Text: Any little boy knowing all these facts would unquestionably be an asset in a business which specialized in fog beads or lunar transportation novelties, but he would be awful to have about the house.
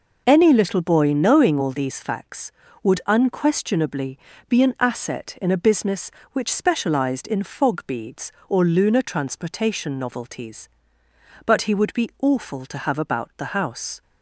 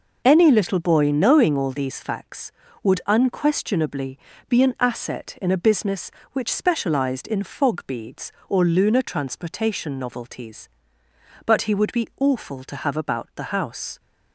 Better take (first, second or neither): neither